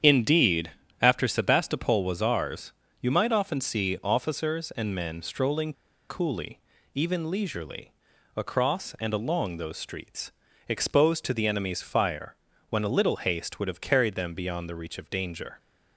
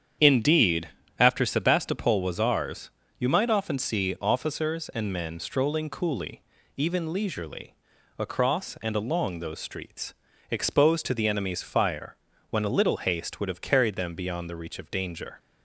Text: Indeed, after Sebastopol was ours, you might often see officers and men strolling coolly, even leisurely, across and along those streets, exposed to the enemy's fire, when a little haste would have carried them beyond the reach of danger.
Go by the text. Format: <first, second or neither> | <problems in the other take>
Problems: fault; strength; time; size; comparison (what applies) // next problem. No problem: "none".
second | starts louder than the rest; strong; until 1.3 s; 8.5 dB; strong in the second // pauses between "strolling" and "coolly"; at 5.7 s; 0.37 s long